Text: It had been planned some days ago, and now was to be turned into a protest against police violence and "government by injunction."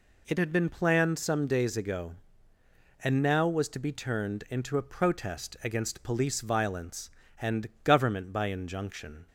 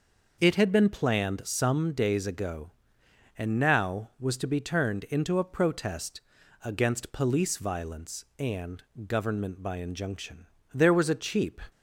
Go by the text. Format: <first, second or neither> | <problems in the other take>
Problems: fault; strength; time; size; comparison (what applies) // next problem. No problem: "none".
first | pauses between "protest" and "against"; at 6.2 s; 0.42 s long // pauses between "and" and "government"; slight; at 8.8 s; 0.24 s long // goes on to say "There was a cheap"; noticeable; from 10.7 s on; 0.88 s long